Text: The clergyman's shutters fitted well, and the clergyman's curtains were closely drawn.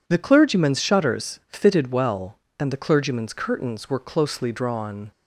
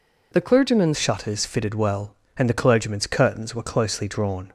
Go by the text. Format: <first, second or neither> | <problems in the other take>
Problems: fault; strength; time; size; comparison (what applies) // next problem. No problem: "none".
first | changes voice at "shutters"; from 0.9 s on; 3.6 s long